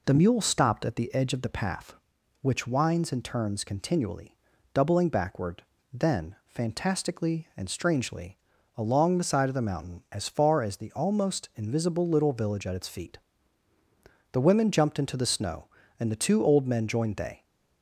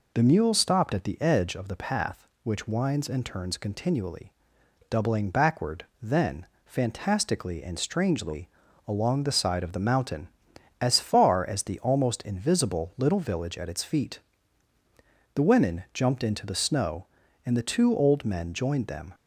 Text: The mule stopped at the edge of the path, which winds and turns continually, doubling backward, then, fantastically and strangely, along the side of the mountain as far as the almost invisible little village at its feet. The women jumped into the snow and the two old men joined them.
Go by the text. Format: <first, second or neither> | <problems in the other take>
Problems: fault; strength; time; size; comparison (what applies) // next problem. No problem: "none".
second | says "they" for "them"; at 17.1 s